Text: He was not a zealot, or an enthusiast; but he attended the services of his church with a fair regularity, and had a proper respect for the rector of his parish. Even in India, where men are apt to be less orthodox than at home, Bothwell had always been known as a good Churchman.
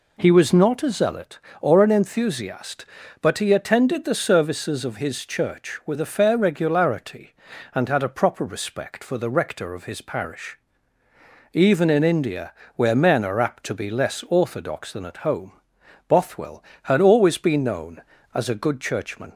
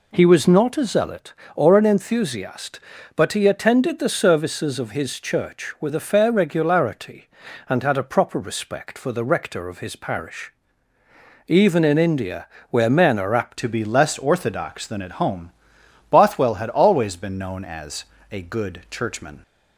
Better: first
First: none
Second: changes voice at "to"; from 13.5 s on; 5.9 s long // pauses between "as" and "a"; slight; at 18.0 s; 0.26 s long

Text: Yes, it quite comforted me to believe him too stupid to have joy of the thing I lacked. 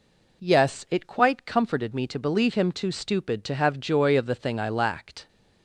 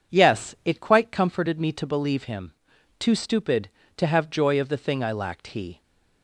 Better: first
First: none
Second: pauses between "him" and "too"; noticeable; at 2.5 s; 0.46 s long // goes on to say "He"; slight; from 5.4 s on; 0.34 s long

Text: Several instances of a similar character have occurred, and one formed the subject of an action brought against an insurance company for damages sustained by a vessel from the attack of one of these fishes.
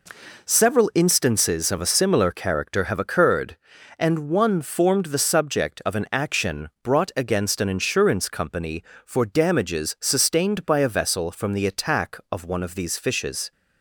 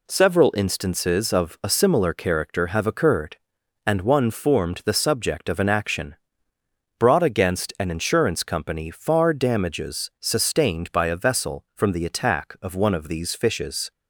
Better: first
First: none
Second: pauses between "action" and "brought"; noticeable; at 6.1 s; 0.82 s long // says "far" for "for"; at 8.8 s

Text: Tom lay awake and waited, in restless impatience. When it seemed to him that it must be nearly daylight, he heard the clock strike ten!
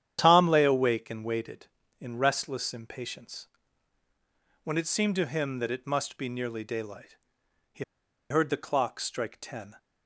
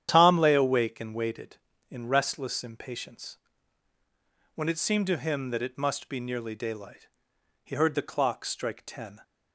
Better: second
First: starts louder than the rest; strong; until 1.2 s; 10 dB // pauses between "he" and "heard"; noticeable; at 7.8 s; 0.47 s long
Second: starts louder than the rest; strong; until 1.1 s; 10 dB

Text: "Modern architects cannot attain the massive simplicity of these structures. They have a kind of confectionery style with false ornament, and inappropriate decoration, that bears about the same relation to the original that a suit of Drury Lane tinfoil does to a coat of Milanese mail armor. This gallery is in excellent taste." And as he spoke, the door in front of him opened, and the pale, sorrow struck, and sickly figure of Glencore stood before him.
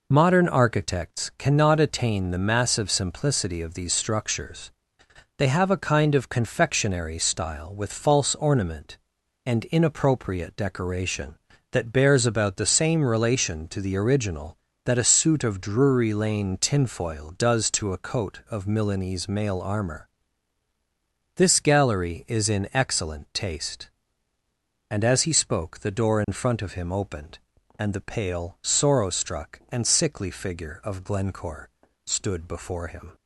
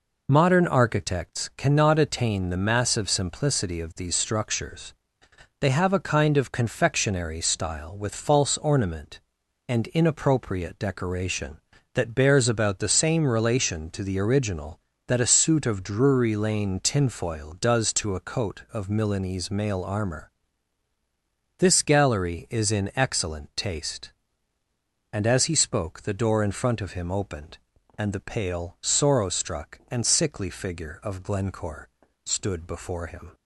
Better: neither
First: pauses between "Glencore" and "stood"; slight; at 31.6 s; 0.36 s long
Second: pauses between "Glencore" and "stood"; slight; at 31.8 s; 0.36 s long

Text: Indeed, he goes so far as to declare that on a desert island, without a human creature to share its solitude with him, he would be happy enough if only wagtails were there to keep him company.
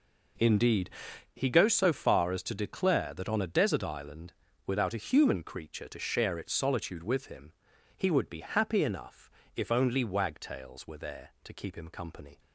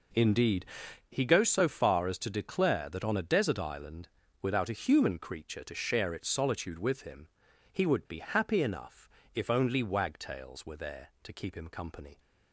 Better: neither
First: pauses between "enough" and "if"; slight; at 9.3 s; 0.24 s long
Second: pauses between "enough" and "if"; slight; at 9.0 s; 0.24 s long

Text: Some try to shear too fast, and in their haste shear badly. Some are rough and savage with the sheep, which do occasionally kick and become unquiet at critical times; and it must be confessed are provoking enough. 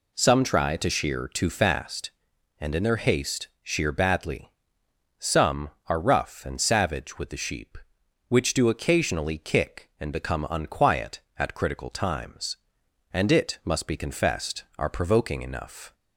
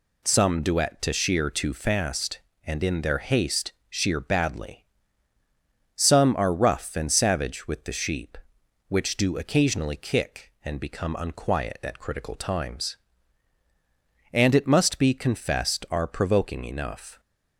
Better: first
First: pauses between "haste" and "shear"; slight; at 3.4 s; 0.16 s long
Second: says "duet" for "try"; at 0.6 s // pauses between "haste" and "shear"; slight; at 3.7 s; 0.16 s long

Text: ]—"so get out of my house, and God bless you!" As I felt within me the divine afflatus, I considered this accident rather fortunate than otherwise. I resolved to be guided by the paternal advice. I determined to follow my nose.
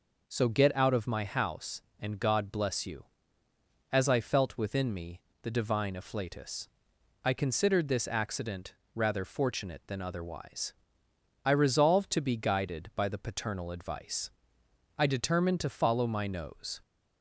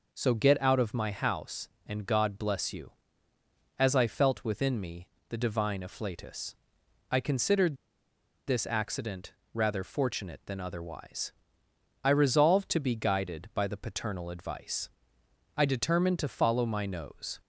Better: first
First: pauses between "me" and "the"; slight; at 5.2 s; 0.22 s long // pauses between "accident" and "rather"; slight; at 8.7 s; 0.20 s long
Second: pauses between "me" and "the"; slight; at 5.0 s; 0.22 s long // pauses between "considered" and "this"; noticeable; at 7.7 s; 0.71 s long // pauses between "accident" and "rather"; slight; at 9.3 s; 0.20 s long

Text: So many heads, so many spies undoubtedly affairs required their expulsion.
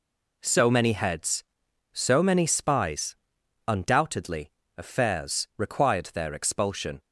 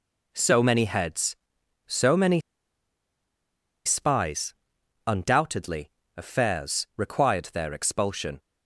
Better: first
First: pauses between "spies" and "undoubtedly"; noticeable; at 3.1 s; 0.51 s long // pauses between "undoubtedly" and "affairs"; slight; at 4.5 s; 0.26 s long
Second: pauses between "many" and "spies"; strong; at 2.3 s; 1.4 s long // pauses between "spies" and "undoubtedly"; noticeable; at 4.5 s; 0.52 s long // pauses between "undoubtedly" and "affairs"; slight; at 5.8 s; 0.26 s long

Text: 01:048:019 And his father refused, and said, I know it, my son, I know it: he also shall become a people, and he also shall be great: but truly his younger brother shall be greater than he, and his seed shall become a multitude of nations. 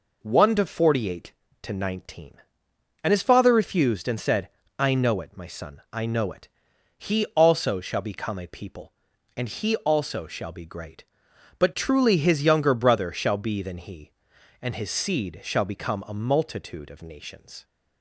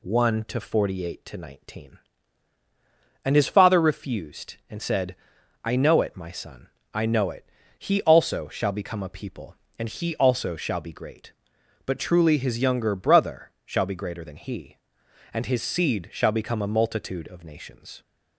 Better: second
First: skips "greater"; at 13.6 s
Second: none

